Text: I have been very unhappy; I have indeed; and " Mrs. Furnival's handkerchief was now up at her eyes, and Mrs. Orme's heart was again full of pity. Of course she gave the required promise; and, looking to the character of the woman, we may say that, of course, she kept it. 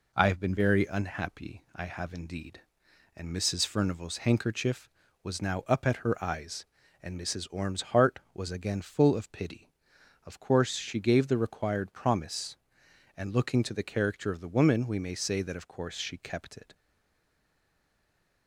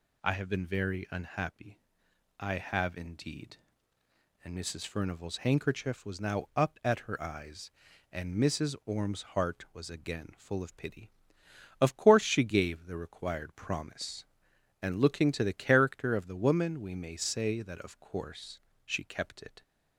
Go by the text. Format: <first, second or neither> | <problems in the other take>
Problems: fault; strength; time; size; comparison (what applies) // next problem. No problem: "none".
second | stays silent after the last word; noticeable; from 16.7 s on; 1.7 s long